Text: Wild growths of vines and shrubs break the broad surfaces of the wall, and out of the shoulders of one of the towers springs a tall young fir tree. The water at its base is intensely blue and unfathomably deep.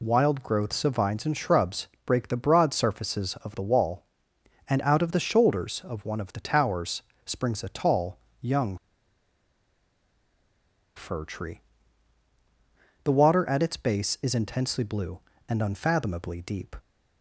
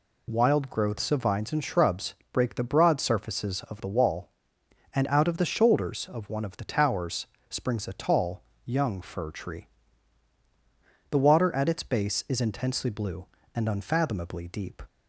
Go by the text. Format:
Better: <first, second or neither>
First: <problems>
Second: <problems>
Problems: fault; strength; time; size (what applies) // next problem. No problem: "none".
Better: second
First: pauses between "shrubs" and "break"; slight; at 1.8 s; 0.20 s long // pauses between "towers" and "springs"; slight; at 7.0 s; 0.22 s long // pauses between "tall" and "young"; slight; at 8.1 s; 0.22 s long // pauses between "young" and "fir"; strong; at 8.7 s; 2.2 s long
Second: pauses between "shrubs" and "break"; slight; at 2.1 s; 0.20 s long // pauses between "towers" and "springs"; slight; at 7.2 s; 0.22 s long // pauses between "tall" and "young"; slight; at 8.4 s; 0.22 s long